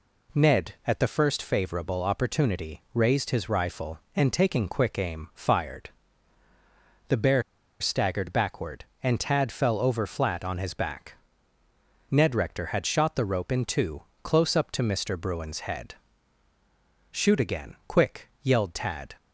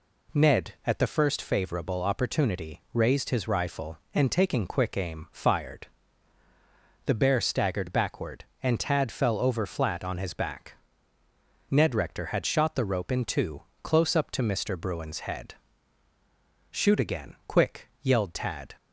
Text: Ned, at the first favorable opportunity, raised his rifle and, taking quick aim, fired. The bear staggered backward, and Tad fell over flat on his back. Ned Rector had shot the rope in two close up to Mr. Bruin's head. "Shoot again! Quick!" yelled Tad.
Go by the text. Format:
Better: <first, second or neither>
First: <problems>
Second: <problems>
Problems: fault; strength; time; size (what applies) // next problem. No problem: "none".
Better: second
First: pauses between "bear" and "staggered"; at 7.4 s; 0.37 s long // pauses between "two" and "close"; slight; at 14.0 s; 0.20 s long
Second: pauses between "two" and "close"; slight; at 13.6 s; 0.20 s long